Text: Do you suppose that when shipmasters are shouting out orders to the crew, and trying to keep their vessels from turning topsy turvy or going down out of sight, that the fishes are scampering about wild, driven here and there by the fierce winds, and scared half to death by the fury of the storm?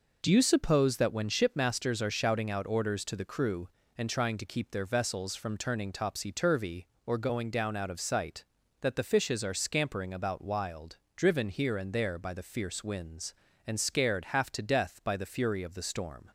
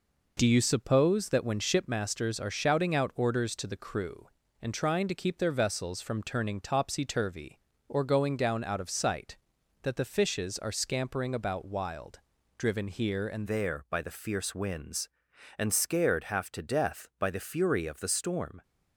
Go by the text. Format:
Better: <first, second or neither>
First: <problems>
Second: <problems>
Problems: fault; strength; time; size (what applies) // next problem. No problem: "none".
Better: first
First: none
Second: changes voice at "there"; from 13.4 s on; 5.2 s long